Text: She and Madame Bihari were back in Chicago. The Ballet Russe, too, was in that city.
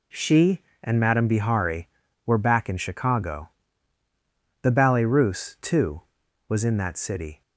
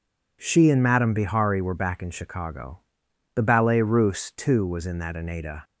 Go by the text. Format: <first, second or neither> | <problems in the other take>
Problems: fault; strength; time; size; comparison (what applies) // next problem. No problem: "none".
first | says "aneda" for "city"; at 5.1 s